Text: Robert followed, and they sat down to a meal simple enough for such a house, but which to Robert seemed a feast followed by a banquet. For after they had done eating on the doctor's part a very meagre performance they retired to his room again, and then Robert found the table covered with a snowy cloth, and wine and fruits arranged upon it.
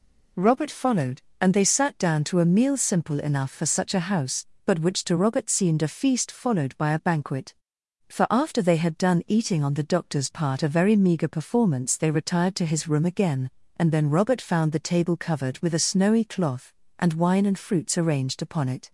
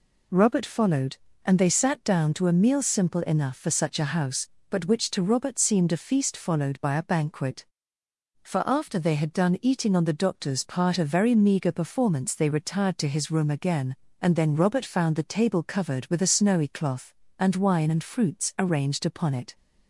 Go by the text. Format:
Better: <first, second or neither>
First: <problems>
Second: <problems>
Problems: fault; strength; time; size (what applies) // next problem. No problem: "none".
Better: neither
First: none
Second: none